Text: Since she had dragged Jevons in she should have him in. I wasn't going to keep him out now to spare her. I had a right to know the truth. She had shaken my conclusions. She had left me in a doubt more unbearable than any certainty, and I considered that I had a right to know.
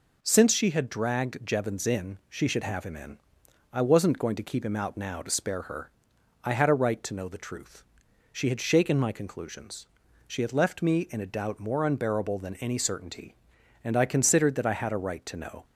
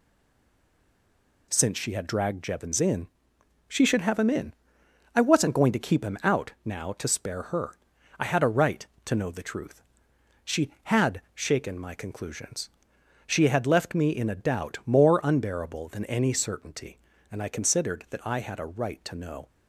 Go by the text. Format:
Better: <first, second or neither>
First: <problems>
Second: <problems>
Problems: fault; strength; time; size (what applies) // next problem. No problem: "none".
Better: first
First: none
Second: stays silent before the first word; noticeable; until 1.5 s; 1.5 s long // pauses between "in" and "she"; noticeable; at 3.0 s; 0.64 s long